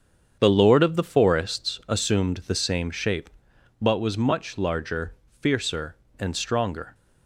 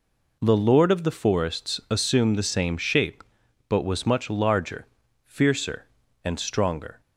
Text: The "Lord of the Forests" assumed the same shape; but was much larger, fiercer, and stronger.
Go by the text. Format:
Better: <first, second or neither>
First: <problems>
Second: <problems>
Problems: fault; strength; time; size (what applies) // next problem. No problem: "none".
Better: second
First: starts louder than the rest; strong; until 1.8 s; 7.5 dB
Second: none